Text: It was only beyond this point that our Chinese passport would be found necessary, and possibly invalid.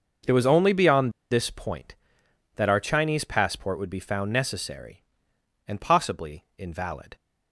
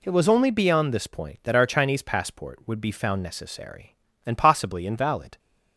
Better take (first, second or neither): second